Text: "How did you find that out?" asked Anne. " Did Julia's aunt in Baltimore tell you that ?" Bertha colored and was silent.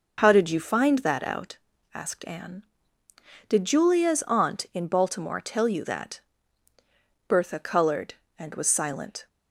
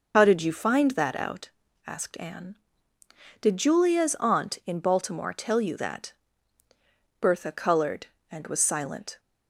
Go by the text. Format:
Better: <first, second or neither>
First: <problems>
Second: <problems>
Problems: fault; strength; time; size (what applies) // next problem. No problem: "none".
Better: first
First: none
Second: loses the start of "How"; at 0.1 s; 45 ms